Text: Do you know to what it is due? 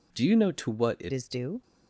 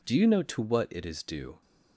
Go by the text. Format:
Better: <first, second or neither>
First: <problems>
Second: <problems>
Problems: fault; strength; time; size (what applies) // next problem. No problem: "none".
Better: second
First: changes voice at "is"; from 1.1 s on; 0.5 s long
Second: none